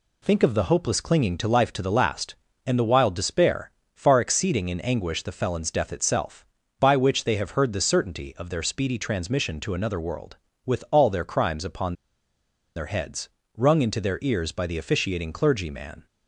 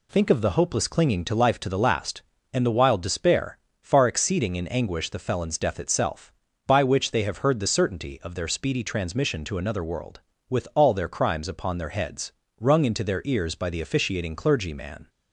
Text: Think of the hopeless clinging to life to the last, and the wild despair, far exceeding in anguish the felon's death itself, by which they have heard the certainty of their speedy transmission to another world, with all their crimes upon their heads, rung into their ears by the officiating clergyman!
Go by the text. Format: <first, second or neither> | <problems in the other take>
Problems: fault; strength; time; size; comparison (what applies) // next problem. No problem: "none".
second | pauses between "upon" and "their"; noticeable; at 11.9 s; 0.82 s long